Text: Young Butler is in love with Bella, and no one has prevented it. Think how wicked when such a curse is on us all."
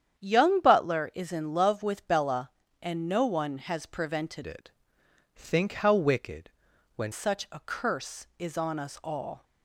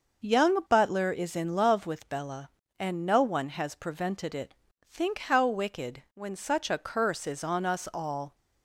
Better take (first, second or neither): second